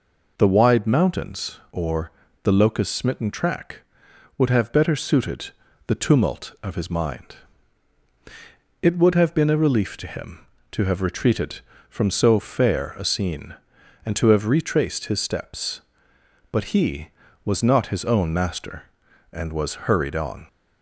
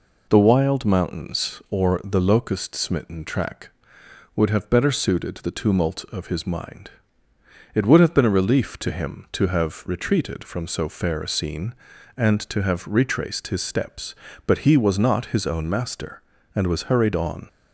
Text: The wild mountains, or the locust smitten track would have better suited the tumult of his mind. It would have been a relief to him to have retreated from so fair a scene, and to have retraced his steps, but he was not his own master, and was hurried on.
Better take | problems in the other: second | says "wide" for "wild"; at 0.4 s // pauses between "or" and "the"; slight; at 2.0 s; 0.32 s long // pauses between "suited" and "the"; slight; at 5.5 s; 0.34 s long

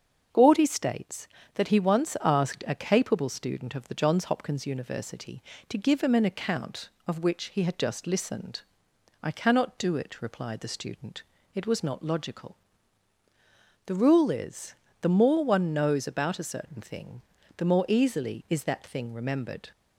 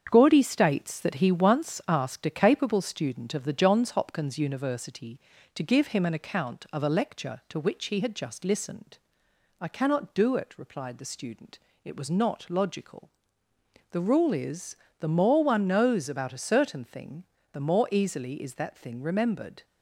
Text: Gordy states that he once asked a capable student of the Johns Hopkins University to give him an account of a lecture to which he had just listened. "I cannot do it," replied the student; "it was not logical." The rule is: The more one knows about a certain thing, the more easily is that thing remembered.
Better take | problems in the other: second | starts louder than the rest; until 1.5 s; 7 dB; strong in the second // skips "a lecture to"; at 7.2 s

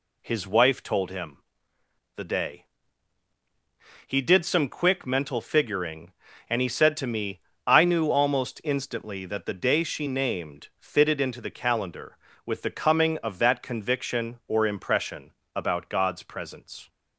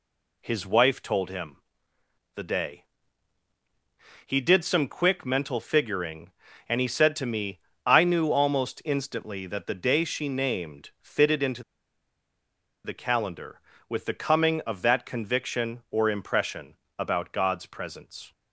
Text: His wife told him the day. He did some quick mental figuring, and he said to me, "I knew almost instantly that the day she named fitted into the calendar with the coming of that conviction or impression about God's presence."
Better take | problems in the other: first | pauses between "him" and "the"; noticeable; at 1.5 s; 0.78 s long; noticeable in the first // pauses between "into" and "the"; at 11.6 s; 1.2 s long // pauses between "impression" and "about"; slight; at 16.7 s; 0.22 s long; slight in the first

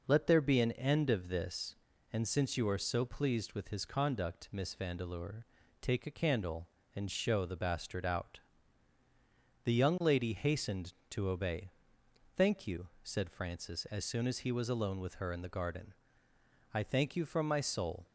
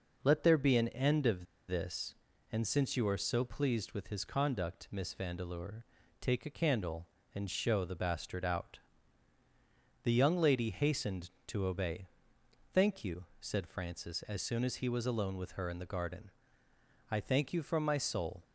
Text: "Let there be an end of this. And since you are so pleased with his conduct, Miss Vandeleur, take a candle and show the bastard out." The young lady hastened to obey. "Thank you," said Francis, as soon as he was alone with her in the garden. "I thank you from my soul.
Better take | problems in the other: first | pauses between "of" and "this"; slight; at 1.4 s; 0.23 s long

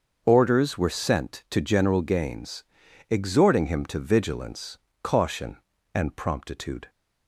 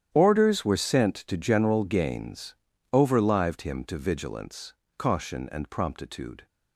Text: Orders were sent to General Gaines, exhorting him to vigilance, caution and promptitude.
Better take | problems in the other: first | starts louder than the rest; strong; until 1.1 s; 10 dB; also in the first // says "overlived" for "exhorting"; at 2.9 s

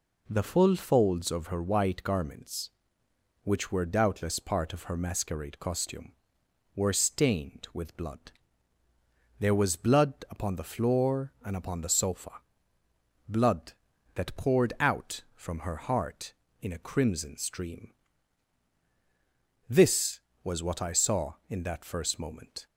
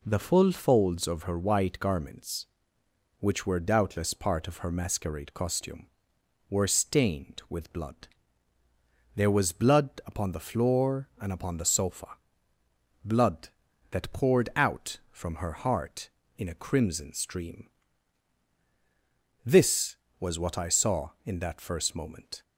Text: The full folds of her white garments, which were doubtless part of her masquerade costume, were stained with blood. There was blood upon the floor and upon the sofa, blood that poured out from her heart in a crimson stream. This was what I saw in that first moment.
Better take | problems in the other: neither | pauses between "blood" and "upon"; slight; the same in both

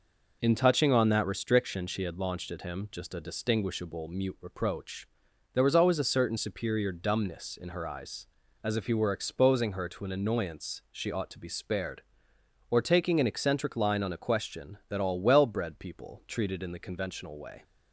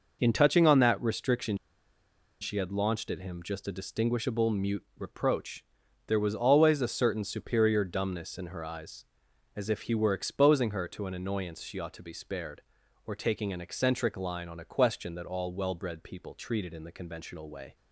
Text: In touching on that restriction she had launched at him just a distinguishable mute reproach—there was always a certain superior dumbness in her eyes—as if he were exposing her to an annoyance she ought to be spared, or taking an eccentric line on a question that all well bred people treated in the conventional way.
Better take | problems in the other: first | pauses between "restriction" and "she"; noticeable; at 1.5 s; 0.85 s long

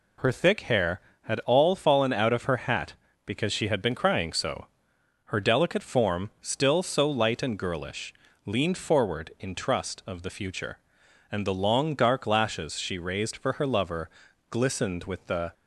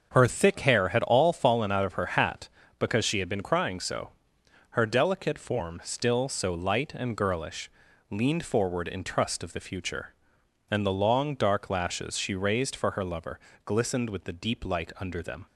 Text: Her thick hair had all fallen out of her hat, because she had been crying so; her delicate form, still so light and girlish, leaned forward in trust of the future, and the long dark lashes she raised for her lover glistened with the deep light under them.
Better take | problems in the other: second | pauses between "lover" and "glistened"; at 14.0 s; 0.42 s long; slight in the second // stops before "deep light under them"; at 15.5 s

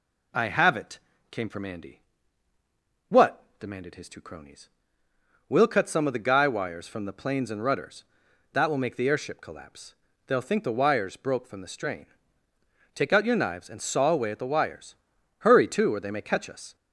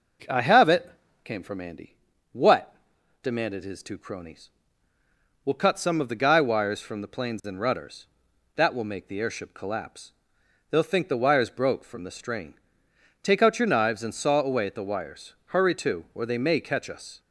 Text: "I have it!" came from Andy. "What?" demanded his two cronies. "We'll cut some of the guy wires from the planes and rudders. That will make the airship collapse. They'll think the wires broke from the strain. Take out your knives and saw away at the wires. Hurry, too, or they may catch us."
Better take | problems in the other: neither | none

